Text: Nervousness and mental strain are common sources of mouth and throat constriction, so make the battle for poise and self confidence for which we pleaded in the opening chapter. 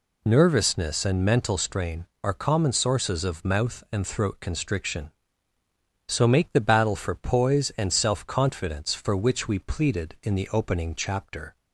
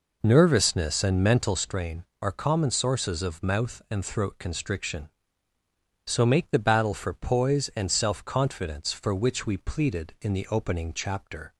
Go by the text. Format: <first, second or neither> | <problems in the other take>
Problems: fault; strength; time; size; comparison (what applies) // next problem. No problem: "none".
first | starts louder than the rest; noticeable; until 1.6 s; 4.5 dB